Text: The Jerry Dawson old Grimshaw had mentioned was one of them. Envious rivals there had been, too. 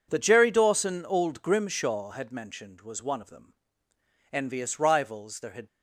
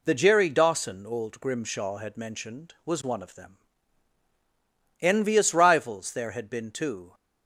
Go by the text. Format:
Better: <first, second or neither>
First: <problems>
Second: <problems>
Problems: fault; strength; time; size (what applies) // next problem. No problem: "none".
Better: second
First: stops before "been too"; at 5.6 s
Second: none